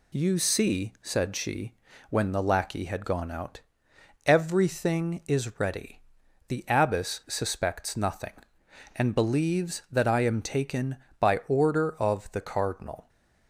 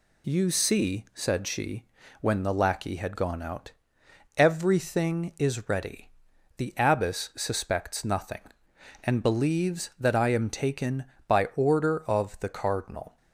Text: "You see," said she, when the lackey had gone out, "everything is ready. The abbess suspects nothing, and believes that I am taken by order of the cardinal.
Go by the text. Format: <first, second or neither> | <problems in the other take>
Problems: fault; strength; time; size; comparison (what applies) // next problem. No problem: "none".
neither | none